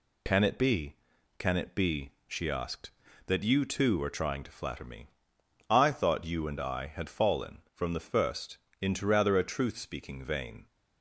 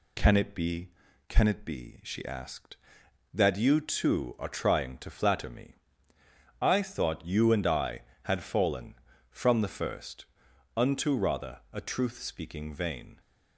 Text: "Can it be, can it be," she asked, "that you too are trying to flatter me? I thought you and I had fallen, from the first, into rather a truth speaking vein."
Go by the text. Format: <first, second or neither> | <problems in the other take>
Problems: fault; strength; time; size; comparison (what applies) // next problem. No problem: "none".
first | says "unto" for "into"; at 10.7 s